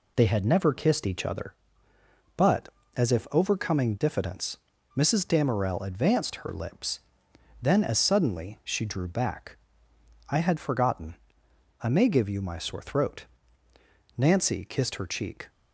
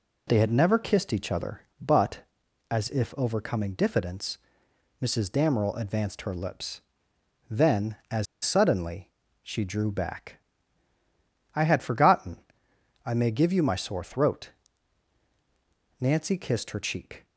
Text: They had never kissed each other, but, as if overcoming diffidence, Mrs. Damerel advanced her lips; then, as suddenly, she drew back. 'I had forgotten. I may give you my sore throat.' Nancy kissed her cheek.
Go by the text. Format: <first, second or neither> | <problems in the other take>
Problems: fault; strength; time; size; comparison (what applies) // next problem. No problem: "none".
first | pauses between "as" and "suddenly"; slight; at 8.2 s; 0.19 s long